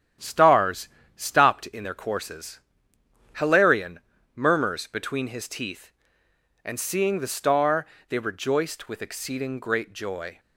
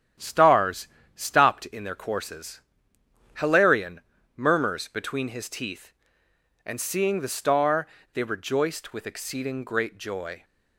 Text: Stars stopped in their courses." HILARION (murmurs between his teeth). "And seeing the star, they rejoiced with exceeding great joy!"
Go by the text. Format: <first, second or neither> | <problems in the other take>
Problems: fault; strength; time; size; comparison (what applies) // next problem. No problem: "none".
neither | starts louder than the rest; strong; the same in both // pauses between "Stars" and "stopped"; slight; the same in both